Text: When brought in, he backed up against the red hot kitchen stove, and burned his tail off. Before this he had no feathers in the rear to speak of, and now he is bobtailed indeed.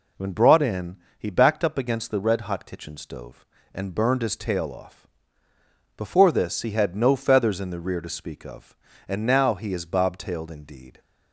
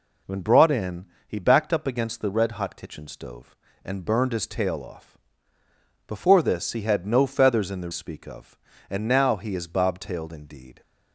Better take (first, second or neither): first